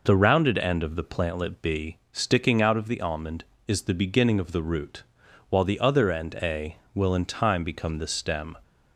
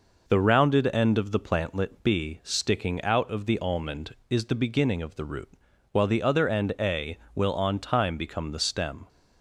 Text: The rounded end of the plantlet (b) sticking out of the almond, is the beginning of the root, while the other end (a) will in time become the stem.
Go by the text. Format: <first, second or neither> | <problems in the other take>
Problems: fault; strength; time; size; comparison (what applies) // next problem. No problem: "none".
first | says "on" for "in"; at 7.5 s